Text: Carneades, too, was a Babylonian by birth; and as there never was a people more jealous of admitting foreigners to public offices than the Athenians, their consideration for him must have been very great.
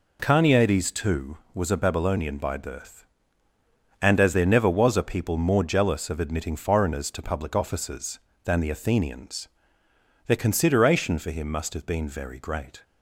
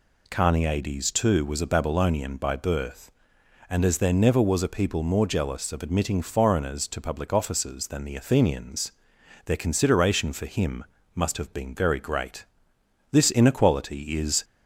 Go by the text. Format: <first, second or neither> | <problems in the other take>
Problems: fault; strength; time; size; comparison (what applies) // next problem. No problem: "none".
first | pauses between "him" and "must"; slight; at 10.8 s; 0.30 s long // goes on to say "This inequality is"; from 13.1 s on; 1.3 s long